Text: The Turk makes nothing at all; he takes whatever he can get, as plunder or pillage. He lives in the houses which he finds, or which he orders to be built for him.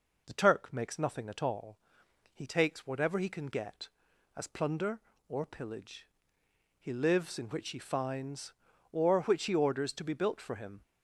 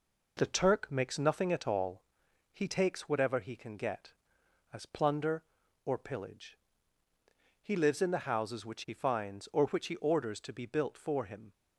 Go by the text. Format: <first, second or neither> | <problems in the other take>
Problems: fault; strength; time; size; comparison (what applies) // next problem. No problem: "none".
second | skips "the houses"; at 7.4 s